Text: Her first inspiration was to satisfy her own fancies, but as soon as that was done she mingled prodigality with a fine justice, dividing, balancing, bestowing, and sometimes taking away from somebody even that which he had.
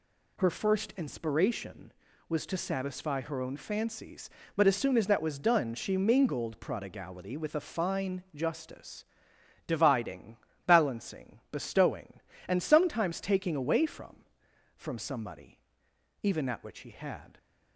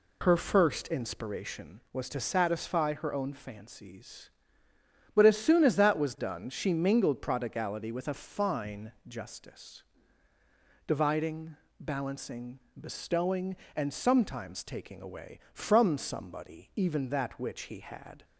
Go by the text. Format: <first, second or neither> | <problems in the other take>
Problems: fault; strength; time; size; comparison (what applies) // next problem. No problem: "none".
second | says "from" twice; at 14.7 s // pauses between "somebody" and "even"; noticeable; at 15.5 s; 0.64 s long